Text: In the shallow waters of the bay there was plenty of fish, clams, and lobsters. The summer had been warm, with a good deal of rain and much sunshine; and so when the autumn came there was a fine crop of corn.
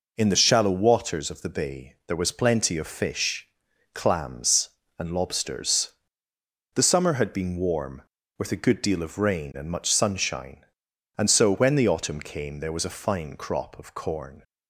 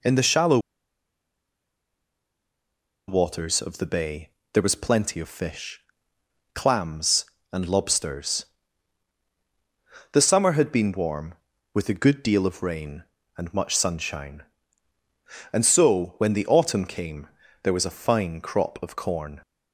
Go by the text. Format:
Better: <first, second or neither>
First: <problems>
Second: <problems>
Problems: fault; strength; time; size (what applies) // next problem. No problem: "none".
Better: first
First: none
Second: pauses between "shallow" and "waters"; strong; at 0.5 s; 2.4 s long // pauses between "bay" and "there"; slight; at 4.2 s; 0.24 s long // pauses between "came" and "there"; slight; at 17.2 s; 0.36 s long